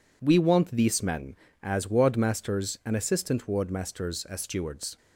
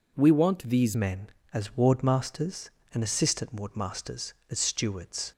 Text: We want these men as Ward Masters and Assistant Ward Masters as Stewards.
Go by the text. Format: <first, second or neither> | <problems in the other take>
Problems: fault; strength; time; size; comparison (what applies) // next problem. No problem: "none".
first | changes voice at "men"; from 0.9 s on; 4.4 s long